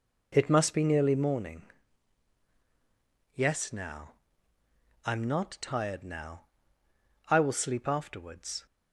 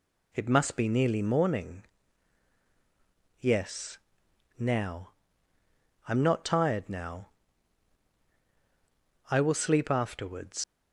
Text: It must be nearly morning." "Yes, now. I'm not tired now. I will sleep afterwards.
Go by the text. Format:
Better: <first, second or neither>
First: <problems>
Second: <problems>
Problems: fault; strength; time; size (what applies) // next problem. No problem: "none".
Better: first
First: none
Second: leaves "afterwards" unfinished; at 10.6 s; 100 ms